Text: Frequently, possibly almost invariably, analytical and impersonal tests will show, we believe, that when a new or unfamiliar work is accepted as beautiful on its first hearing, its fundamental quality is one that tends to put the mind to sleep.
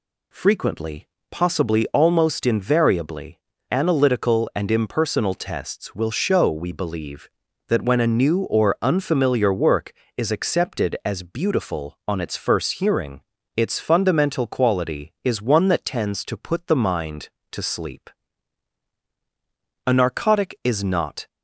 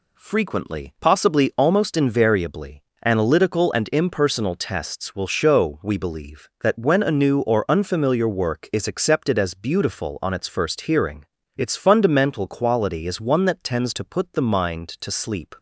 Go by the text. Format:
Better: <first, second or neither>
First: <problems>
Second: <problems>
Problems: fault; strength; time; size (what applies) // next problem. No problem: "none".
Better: second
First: goes on to say "A narcotic is not"; from 19.8 s on; 1.4 s long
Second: none